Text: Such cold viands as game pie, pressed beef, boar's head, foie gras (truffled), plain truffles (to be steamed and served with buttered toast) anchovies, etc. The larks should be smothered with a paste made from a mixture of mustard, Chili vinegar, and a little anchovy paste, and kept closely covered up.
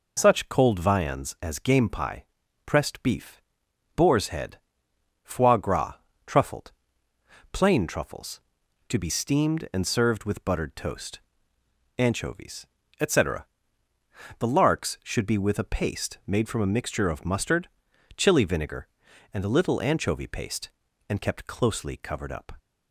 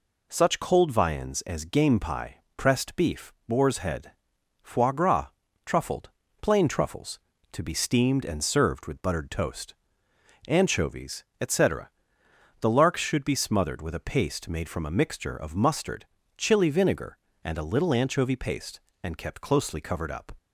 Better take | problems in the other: second | skips "smothered"; at 15.3 s

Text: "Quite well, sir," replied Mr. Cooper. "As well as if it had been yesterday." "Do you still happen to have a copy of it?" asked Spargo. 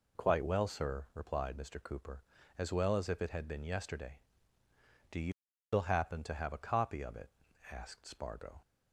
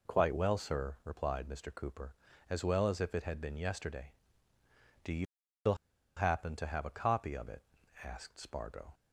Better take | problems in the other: first | pauses between "you" and "still"; at 5.2 s; 0.38 s long; also in the first // pauses between "still" and "happen"; at 5.7 s; 0.42 s long

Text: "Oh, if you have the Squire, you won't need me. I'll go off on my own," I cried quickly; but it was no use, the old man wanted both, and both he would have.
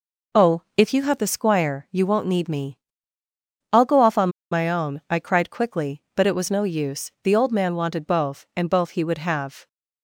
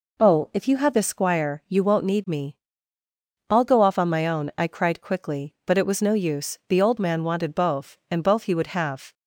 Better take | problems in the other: second | pauses between "on" and "my"; slight; at 4.2 s; 0.22 s long

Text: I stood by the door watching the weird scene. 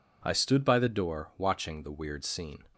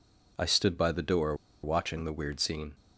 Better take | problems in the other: first | pauses between "door" and "watching"; slight; at 1.3 s; 0.27 s long

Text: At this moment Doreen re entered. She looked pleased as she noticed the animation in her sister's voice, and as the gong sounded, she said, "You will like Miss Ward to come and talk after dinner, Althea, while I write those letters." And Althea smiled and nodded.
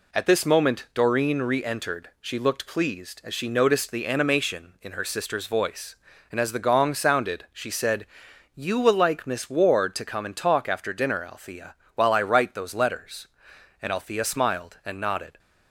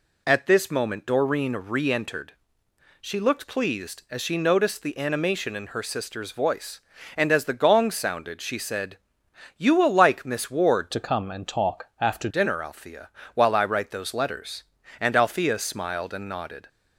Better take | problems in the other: first | changes voice from "to" to "after"; from 10.9 to 12.2 s; 1.3 s long

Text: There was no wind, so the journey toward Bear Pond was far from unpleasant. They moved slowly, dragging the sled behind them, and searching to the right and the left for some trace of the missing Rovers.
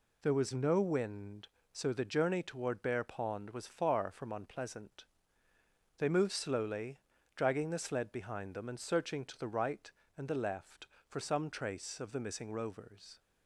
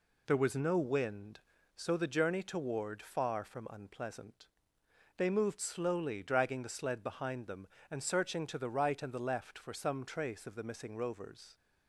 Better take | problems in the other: first | skips "Bear Pond was"; at 2.9 s

